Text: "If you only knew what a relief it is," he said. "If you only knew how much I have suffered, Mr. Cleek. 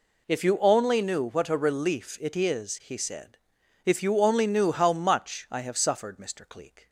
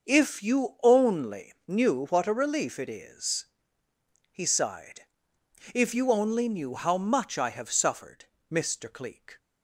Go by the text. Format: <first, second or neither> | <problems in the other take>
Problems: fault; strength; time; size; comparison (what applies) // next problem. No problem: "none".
first | says "sighed" for "said"; at 4.4 s